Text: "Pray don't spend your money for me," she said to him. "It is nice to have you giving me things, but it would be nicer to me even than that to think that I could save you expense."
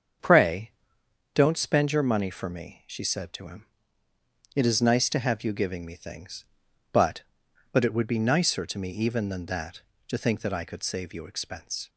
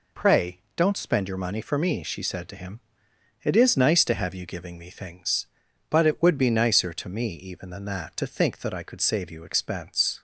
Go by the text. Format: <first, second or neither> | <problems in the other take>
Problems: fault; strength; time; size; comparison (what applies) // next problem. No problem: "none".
second | starts louder than the rest; until 1.8 s; 7 dB // pauses between "Pray" and "don't"; noticeable; at 0.7 s; 0.62 s long // says "but" twice; at 7.7 s